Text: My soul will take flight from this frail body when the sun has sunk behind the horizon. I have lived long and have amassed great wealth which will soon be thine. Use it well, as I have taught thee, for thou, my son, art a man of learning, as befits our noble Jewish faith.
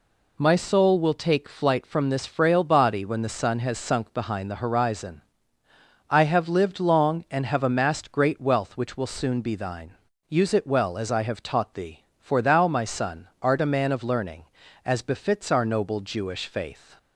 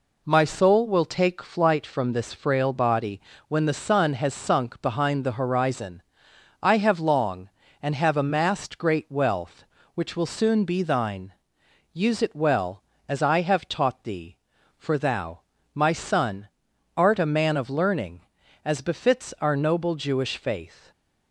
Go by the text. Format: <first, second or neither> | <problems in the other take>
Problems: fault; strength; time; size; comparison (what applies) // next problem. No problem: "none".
first | pauses between "body" and "when"; slight; at 3.2 s; 0.26 s long // skips "lived"; at 6.9 s